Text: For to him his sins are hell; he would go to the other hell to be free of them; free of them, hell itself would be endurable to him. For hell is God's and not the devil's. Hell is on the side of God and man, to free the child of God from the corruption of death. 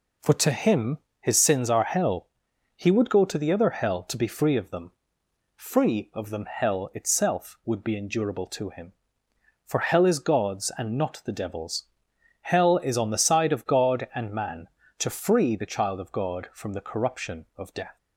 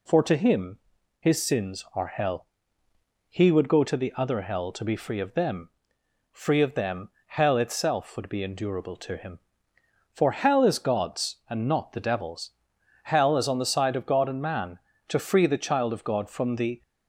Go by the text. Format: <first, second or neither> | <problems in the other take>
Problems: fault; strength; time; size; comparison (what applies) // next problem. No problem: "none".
first | pauses between "him" and "his"; at 0.7 s; 0.40 s long; slight in the first // stops before "corruption of death"; at 16.8 s